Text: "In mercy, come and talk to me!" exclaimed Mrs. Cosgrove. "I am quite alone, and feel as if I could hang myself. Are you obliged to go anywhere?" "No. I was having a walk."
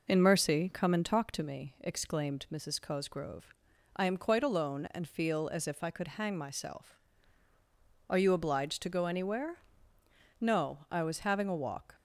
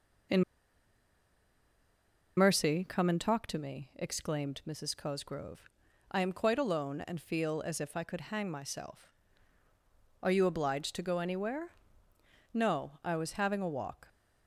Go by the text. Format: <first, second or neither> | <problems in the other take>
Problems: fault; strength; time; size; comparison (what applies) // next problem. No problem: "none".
first | pauses between "In" and "mercy"; strong; at 0.4 s; 1.9 s long